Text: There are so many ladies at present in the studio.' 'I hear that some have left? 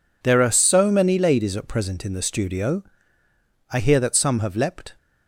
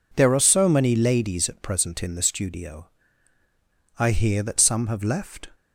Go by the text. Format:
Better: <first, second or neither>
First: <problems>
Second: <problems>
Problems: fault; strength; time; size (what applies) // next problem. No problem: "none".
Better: second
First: says "leapt" for "left"; at 4.5 s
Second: none